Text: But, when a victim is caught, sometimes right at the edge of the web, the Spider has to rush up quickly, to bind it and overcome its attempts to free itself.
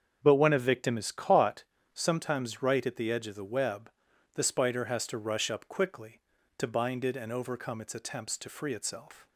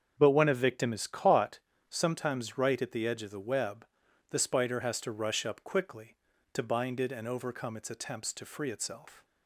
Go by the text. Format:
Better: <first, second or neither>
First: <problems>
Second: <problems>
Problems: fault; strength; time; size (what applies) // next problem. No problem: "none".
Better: neither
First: starts louder than the rest; until 1.2 s; 7 dB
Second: starts louder than the rest; until 1.1 s; 7 dB